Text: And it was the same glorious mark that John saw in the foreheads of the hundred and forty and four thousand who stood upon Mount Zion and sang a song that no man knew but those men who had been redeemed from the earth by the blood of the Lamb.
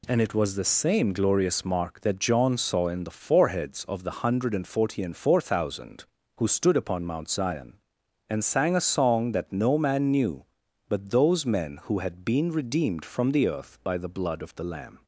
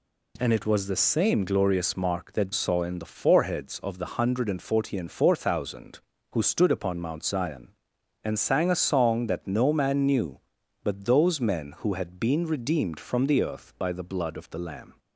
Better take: first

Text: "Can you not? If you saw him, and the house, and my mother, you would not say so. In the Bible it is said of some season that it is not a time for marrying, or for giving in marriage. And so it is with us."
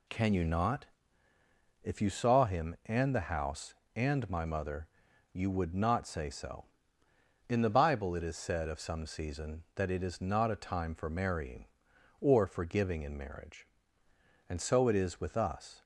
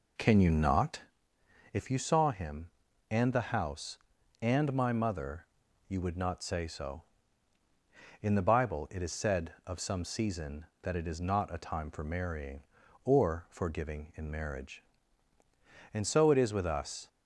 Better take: first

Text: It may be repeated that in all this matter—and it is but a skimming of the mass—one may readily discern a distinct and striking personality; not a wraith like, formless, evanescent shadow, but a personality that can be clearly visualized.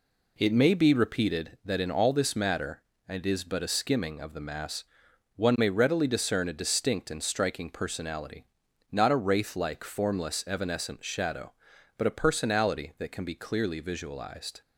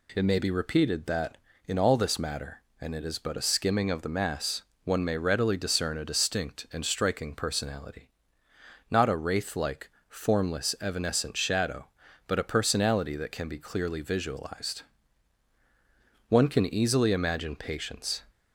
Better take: first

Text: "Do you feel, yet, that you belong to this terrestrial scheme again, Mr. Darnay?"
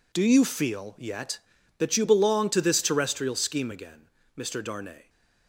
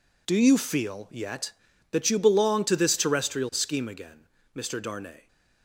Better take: neither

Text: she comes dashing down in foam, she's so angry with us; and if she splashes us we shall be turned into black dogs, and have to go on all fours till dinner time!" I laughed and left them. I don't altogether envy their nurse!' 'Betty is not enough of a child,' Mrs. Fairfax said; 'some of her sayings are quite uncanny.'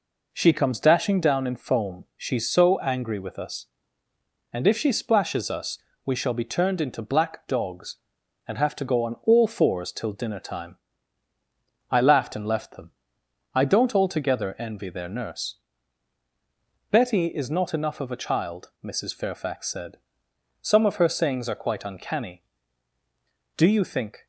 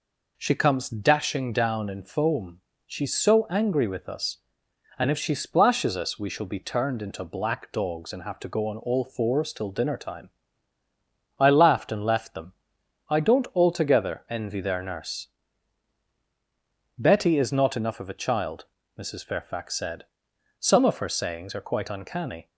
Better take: second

